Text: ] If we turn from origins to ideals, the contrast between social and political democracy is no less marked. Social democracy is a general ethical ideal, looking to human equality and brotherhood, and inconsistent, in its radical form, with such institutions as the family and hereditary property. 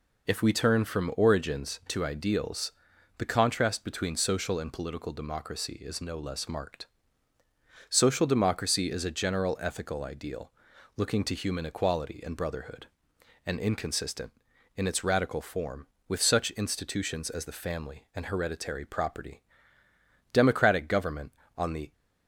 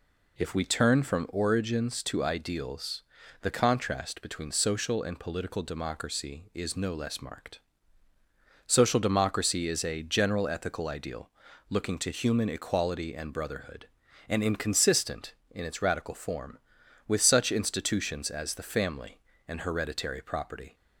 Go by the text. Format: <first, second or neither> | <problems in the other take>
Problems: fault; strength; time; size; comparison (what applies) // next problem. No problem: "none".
second | goes on to say "Democratic government on the"; from 20.3 s on; 1.5 s long